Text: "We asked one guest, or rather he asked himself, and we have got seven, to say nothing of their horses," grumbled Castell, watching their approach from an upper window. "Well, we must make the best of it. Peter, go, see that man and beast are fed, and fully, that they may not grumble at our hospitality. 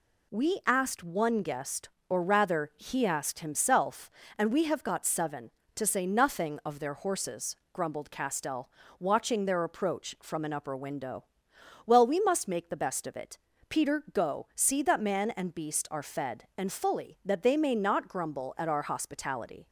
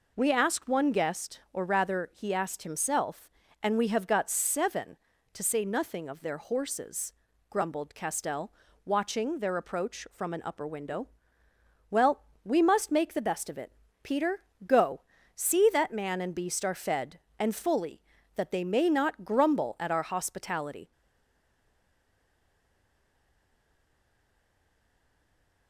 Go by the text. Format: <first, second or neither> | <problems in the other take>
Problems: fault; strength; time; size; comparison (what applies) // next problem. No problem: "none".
first | stays silent after the last word; strong; from 20.9 s on; 4.7 s long